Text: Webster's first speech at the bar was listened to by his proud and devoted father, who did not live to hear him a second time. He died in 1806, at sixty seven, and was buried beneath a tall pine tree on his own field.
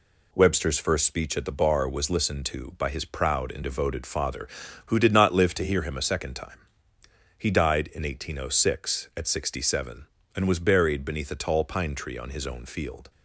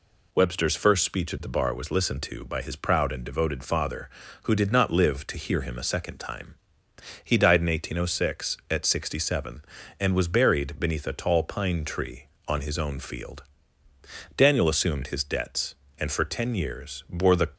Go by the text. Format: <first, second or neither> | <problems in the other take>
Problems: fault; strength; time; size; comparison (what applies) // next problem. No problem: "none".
first | goes on to say "Daniel assumed his debts and for ten years bore the"; strong; from 14.3 s on; 3.1 s long